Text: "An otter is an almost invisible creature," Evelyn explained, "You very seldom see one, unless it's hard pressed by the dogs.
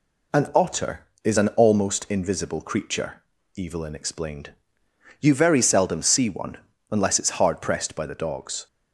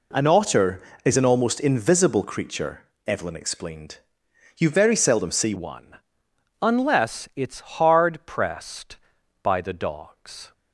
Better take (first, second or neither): first